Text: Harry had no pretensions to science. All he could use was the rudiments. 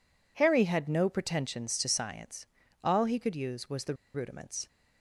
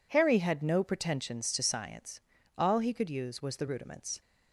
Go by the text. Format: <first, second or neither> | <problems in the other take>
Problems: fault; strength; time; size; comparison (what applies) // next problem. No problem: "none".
second | pauses between "the" and "rudiments"; slight; at 3.9 s; 0.20 s long